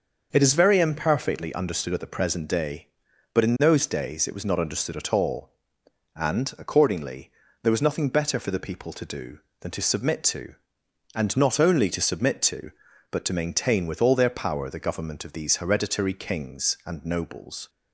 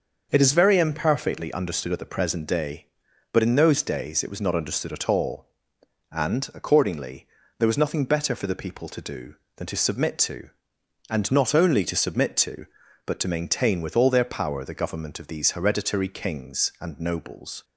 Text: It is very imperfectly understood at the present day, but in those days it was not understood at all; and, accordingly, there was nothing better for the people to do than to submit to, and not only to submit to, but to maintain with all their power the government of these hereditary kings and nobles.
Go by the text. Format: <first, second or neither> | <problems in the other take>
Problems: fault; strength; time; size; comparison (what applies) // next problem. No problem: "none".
neither | starts louder than the rest; the same in both